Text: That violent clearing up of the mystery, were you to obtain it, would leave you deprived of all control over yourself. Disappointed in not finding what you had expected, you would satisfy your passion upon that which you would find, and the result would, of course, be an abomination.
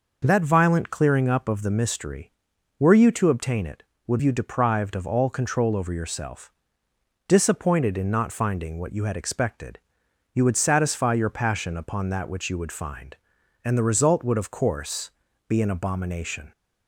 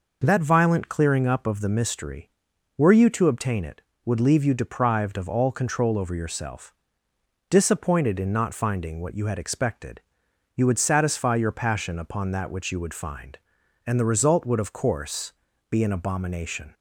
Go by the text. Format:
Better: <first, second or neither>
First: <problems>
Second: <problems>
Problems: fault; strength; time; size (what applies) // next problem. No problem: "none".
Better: second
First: skips "leave"; at 4.2 s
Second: none